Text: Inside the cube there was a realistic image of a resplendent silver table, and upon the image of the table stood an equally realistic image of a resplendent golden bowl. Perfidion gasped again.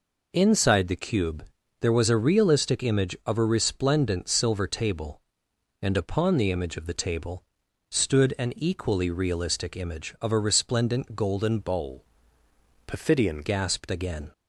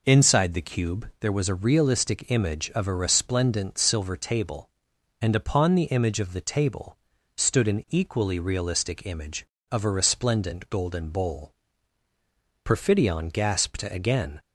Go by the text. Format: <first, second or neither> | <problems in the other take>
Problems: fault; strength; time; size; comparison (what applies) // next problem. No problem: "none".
second | pauses between "cube" and "there"; slight; at 1.4 s; 0.34 s long // pauses between "table" and "stood"; noticeable; at 7.4 s; 0.46 s long; also in the second // changes voice from "bowl" to "Perfidion"; from 11.6 to 13.4 s; 1.8 s long